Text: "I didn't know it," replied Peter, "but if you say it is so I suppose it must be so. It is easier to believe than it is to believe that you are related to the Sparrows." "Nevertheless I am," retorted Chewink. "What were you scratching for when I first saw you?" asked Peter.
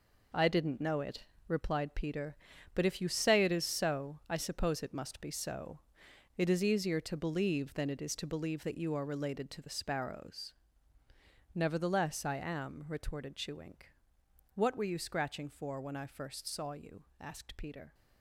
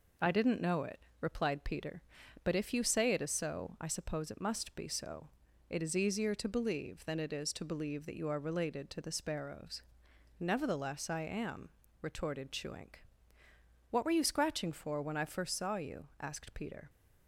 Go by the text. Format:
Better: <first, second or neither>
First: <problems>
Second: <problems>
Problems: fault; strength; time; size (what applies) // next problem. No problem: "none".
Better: second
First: gets quieter; strong; throughout; 10 dB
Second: none